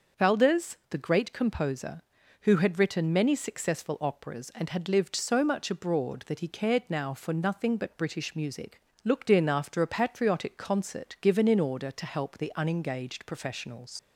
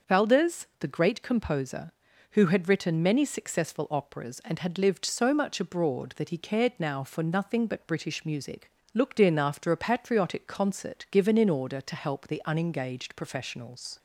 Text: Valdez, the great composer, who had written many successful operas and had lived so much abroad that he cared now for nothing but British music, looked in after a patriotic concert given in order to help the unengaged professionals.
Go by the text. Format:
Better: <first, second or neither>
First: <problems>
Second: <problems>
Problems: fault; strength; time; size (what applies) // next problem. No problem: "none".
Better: second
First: starts louder than the rest; until 1.3 s; 6.5 dB // leaves "professionals" unfinished; at 13.9 s; 90 ms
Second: starts louder than the rest; until 1.1 s; 6.5 dB